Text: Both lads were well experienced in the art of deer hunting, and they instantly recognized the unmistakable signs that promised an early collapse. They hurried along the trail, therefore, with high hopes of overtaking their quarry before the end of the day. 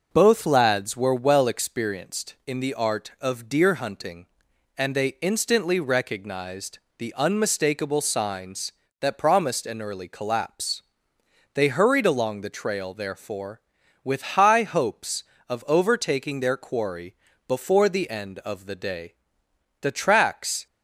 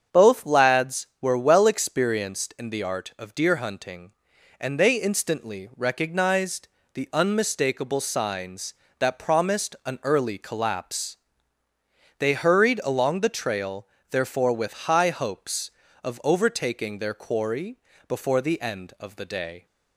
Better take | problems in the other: second | starts louder than the rest; noticeable; until 1.1 s; 6 dB; strong in the second // pauses between "recognized" and "the"; slight; at 6.8 s; 0.18 s long; slight in the second // pauses between "quarry" and "before"; slight; at 17.1 s; 0.34 s long; slight in the second // goes on to say "The tracks"; noticeable; from 19.8 s on; 0.86 s long

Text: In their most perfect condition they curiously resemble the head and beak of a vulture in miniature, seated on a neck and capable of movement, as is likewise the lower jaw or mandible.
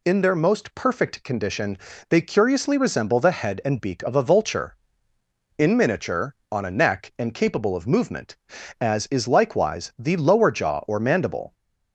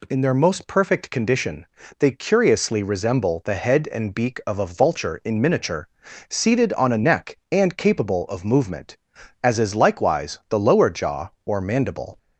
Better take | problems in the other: second | pauses between "condition" and "they"; slight; at 1.7 s; 0.32 s long; slight in the second // skips "seated"; at 6.4 s

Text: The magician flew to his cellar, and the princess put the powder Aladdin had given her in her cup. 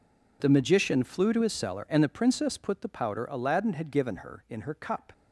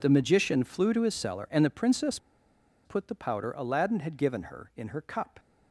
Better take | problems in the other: first | pauses between "princess" and "put"; noticeable; at 2.1 s; 0.67 s long

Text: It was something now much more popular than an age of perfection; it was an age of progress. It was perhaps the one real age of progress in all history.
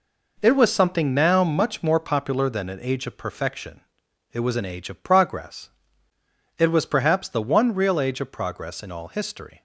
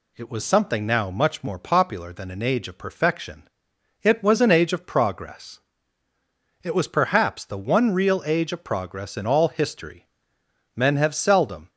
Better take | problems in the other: first | goes on to say "Men have seldom"; noticeable; from 10.7 s on; 0.94 s long

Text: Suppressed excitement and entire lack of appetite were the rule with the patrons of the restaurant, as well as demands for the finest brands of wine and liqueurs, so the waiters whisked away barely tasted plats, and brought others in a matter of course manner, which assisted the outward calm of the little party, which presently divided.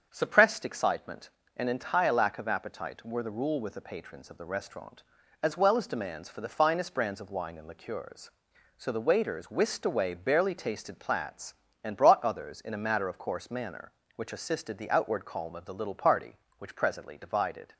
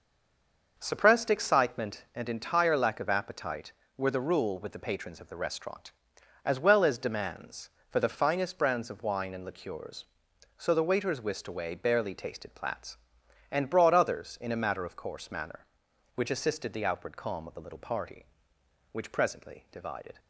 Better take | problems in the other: first | stays silent before the first word; slight; until 0.7 s; 0.7 s long // starts louder than the rest; noticeable; until 1.7 s; 6 dB; also in the first

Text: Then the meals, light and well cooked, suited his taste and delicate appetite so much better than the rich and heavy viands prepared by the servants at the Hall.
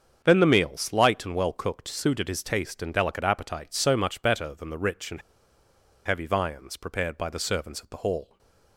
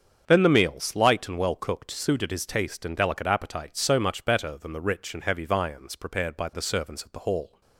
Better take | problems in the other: second | starts louder than the rest; strong; until 1.2 s; 7 dB; strong in the second // pauses between "and" and "heavy"; noticeable; at 5.2 s; 0.84 s long // stays silent after the last word; slight; from 8.2 s on; 0.5 s long

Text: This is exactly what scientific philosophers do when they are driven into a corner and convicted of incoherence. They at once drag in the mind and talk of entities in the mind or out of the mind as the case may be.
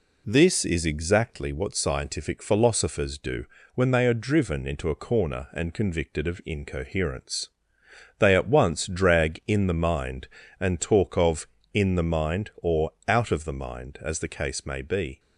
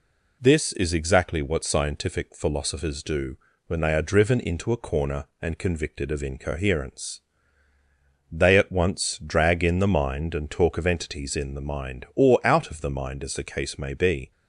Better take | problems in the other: second | pauses between "do" and "when"; slight; at 3.4 s; 0.30 s long; slight in the second // skips "entities"; at 11.5 s // pauses between "or" and "out"; slight; at 12.8 s; 0.18 s long

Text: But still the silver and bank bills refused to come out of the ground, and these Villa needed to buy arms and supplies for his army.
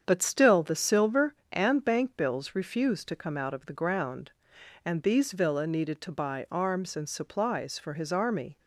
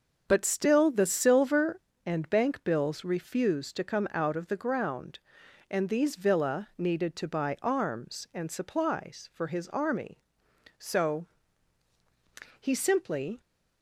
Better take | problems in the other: first | starts louder than the rest; until 1.2 s; 6.5 dB; strong in the first // goes on to say "So he simply"; strong; from 10.7 s on; 2.6 s long

